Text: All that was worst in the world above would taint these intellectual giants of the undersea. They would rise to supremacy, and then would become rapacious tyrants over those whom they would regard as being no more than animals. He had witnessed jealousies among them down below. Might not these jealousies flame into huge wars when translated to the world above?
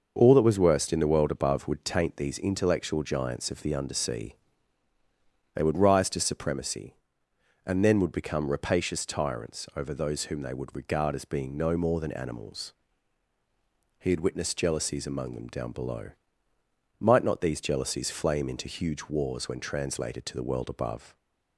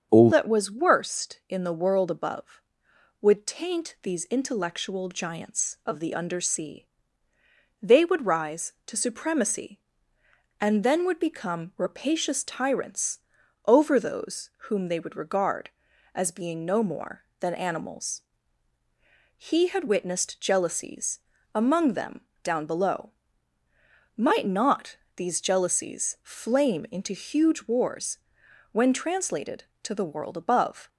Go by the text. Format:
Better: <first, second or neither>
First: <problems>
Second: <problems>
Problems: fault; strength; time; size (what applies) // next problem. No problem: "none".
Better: first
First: starts louder than the rest; noticeable; until 1.1 s; 6 dB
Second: starts louder than the rest; until 1.1 s; 7 dB // changes voice at "that"; from 0.3 s on; 30.5 s long // pauses between "tyrants" and "over"; noticeable; at 13.2 s; 0.46 s long // pauses between "those" and "whom"; slight; at 14.5 s; 0.18 s long // pauses between "jealousies" and "among"; slight; at 21.2 s; 0.34 s long // pauses between "them" and "down"; slight; at 22.2 s; 0.20 s long // pauses between "not" and "these"; slight; at 24.9 s; 0.20 s long // pauses between "wars" and "when"; noticeable; at 28.1 s; 0.54 s long